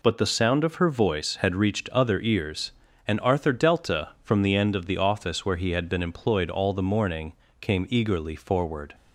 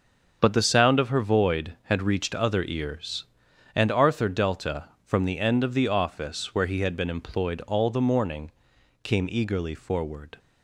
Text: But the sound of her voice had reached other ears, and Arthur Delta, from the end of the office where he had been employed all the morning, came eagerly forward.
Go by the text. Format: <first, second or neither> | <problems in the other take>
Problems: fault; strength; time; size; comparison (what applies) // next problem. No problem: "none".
first | starts louder than the rest; until 1.4 s; 6 dB // says "void" for "voice"; at 1.2 s